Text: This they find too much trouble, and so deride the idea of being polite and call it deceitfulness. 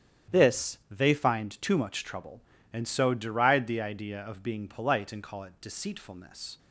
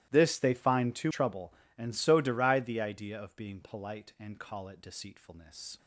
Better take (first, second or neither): first